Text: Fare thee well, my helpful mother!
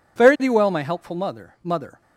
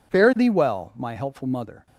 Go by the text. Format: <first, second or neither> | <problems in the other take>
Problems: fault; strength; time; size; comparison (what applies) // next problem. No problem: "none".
second | says "mother" twice; at 1.6 s